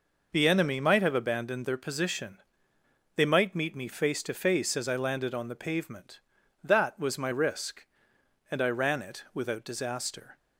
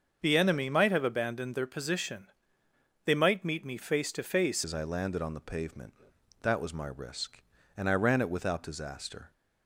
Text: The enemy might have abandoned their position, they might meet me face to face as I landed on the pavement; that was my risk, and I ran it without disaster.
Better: first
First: none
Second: starts louder than the rest; until 1.2 s; 7 dB // changes voice at "as"; from 4.6 s on; 4.7 s long

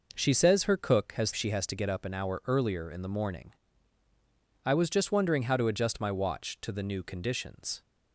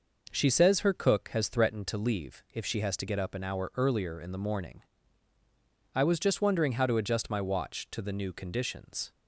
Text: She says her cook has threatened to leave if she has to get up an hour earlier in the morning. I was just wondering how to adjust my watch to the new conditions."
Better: second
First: skips "threatened to leave if"; at 1.3 s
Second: none

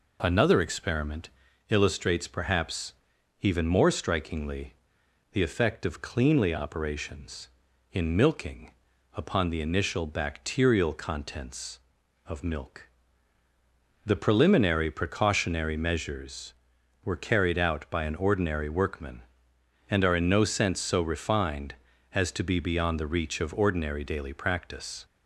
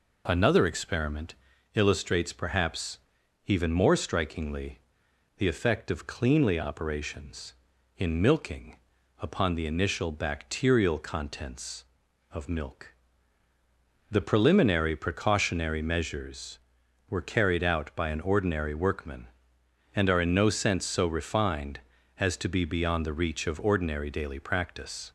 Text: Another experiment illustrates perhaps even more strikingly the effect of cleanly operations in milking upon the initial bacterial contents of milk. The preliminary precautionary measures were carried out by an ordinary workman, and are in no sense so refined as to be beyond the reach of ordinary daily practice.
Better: neither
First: pauses between "experiment" and "illustrates"; at 1.2 s; 0.42 s long // pauses between "perhaps" and "even"; noticeable; at 2.9 s; 0.48 s long // pauses between "strikingly" and "the"; noticeable; at 4.7 s; 0.58 s long // pauses between "milking" and "upon"; at 8.7 s; 0.44 s long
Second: pauses between "experiment" and "illustrates"; at 1.3 s; 0.42 s long // pauses between "perhaps" and "even"; noticeable; at 2.9 s; 0.48 s long // pauses between "strikingly" and "the"; noticeable; at 4.8 s; 0.58 s long // pauses between "milking" and "upon"; at 8.7 s; 0.44 s long

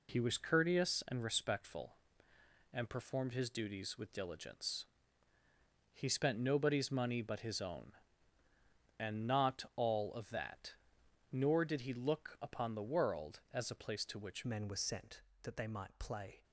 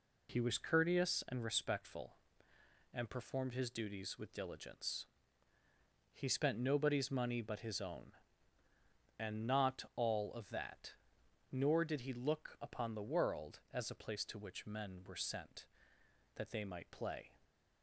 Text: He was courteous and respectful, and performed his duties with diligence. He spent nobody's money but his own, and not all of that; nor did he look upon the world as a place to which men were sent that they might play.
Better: second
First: changes voice at "men"; from 14.4 s on; 2.0 s long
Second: none

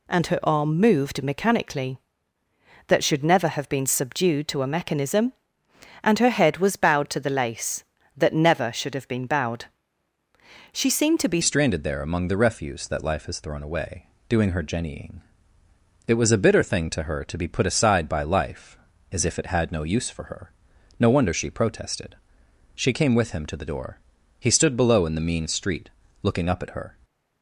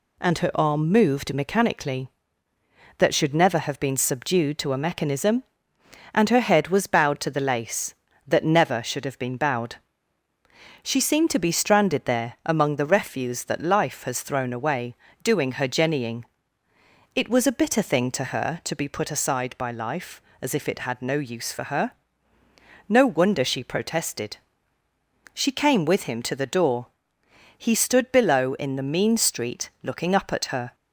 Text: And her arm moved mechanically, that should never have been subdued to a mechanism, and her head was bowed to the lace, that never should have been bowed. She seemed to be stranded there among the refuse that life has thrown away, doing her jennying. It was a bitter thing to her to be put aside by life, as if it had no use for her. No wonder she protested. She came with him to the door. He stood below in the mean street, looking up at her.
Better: second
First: changes voice at "stranded"; from 11.4 s on; 15.5 s long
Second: none

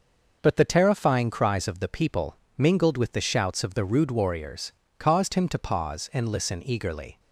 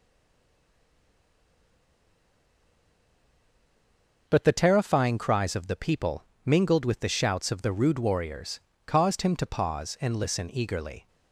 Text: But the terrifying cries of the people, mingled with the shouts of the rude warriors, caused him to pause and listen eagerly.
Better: first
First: none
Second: stays silent before the first word; strong; until 4.2 s; 4.2 s long

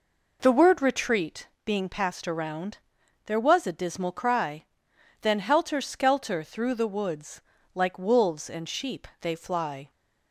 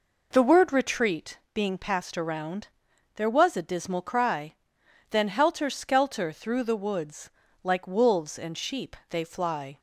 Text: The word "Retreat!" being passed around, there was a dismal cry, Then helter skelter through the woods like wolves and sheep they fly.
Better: neither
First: pauses between "woods" and "like"; slight; at 7.4 s; 0.32 s long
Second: pauses between "woods" and "like"; slight; at 7.3 s; 0.32 s long

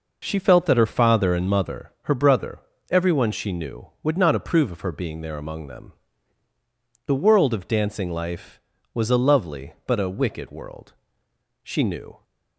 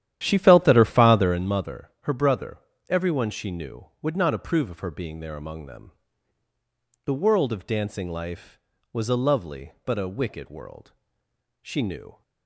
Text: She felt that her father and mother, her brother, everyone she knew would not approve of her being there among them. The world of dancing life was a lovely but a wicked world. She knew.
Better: first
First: none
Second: starts louder than the rest; strong; until 1.5 s; 11 dB

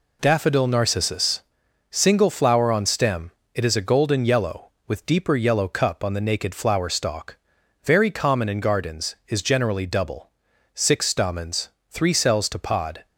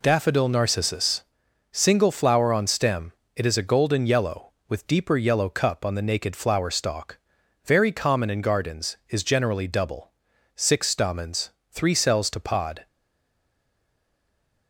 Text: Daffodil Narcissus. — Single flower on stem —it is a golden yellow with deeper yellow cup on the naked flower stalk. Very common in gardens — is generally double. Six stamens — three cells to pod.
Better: first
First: none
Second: stays silent after the last word; noticeable; from 12.8 s on; 1.8 s long

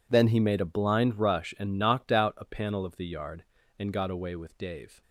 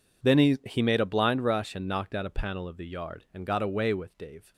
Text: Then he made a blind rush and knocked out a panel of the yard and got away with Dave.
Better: first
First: none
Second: says "he" twice; at 0.6 s

